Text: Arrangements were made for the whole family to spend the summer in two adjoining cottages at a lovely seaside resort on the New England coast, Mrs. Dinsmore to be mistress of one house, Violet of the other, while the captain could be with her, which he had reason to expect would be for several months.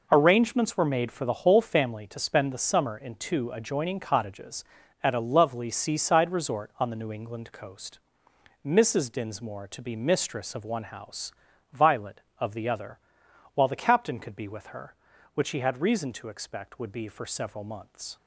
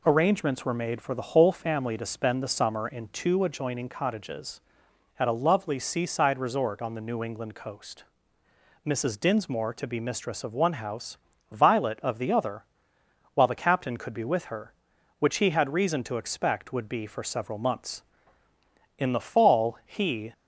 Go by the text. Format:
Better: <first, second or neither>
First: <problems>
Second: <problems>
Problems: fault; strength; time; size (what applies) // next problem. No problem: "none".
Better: first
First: none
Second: goes on to say "In the fall he"; from 18.9 s on; 1.3 s long